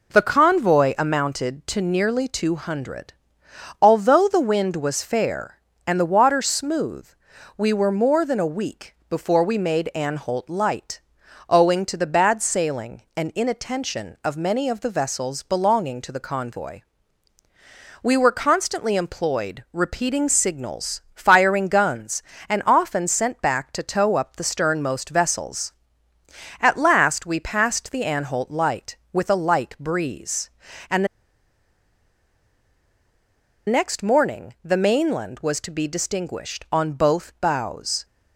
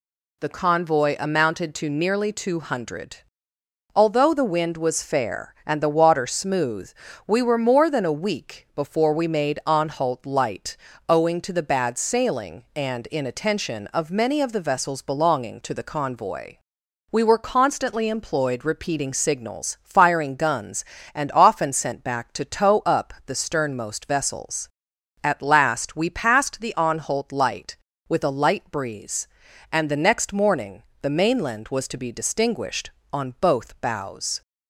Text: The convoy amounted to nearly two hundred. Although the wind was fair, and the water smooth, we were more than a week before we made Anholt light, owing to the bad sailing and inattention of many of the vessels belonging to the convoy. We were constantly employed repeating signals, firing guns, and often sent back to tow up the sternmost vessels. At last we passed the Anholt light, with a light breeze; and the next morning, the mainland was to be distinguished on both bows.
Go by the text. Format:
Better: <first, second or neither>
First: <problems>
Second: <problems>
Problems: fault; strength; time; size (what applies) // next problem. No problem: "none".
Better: second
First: pauses between "the" and "next"; strong; at 31.0 s; 2.6 s long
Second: none